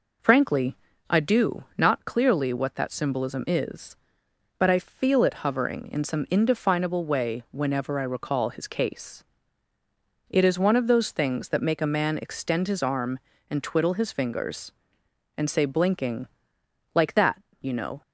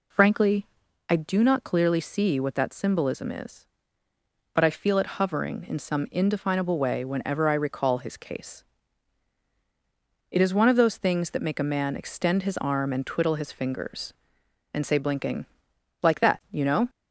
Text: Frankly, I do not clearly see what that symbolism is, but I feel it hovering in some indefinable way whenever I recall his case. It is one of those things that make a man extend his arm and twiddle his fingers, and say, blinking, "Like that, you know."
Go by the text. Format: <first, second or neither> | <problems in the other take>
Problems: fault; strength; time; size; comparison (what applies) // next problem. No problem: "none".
second | skips "see"; at 2.5 s